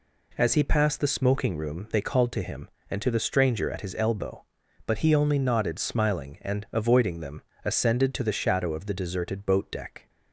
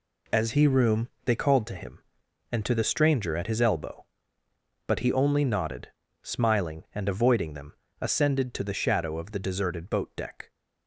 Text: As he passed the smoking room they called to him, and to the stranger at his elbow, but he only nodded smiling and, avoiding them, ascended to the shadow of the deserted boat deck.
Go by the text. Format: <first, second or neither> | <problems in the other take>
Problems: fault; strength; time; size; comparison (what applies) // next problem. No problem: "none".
first | skips "passed the smoking"; at 0.6 s // pauses between "room" and "they"; slight; at 1.0 s; 0.16 s long // pauses between "nodded" and "smiling"; slight; at 5.8 s; 0.32 s long